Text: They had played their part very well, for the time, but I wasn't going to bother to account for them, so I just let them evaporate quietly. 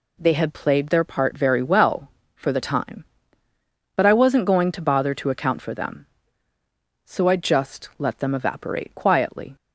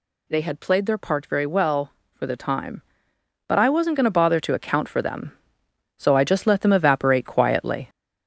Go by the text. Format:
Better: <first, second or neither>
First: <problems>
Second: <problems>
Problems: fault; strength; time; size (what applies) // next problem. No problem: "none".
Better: first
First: none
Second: gets louder; noticeable; throughout; 5 dB